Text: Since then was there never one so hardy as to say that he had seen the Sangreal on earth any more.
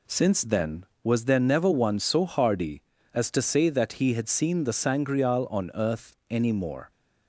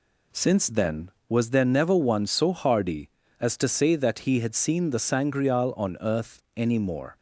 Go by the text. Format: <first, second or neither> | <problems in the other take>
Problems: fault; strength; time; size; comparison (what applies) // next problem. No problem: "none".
neither | pauses between "earth" and "any"; slight; the same in both